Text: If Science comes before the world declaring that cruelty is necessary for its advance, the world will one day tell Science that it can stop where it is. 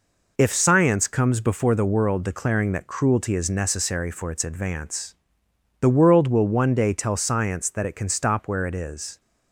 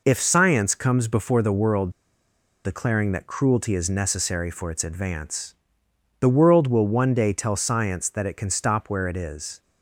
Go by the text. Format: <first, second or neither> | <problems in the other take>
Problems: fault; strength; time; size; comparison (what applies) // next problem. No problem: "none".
first | pauses between "world" and "declaring"; noticeable; at 1.9 s; 0.73 s long